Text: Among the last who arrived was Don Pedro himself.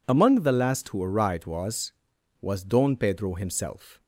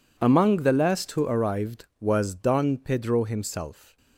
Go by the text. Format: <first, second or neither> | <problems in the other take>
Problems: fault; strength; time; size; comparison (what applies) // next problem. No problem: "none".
second | says "was" twice; at 2.4 s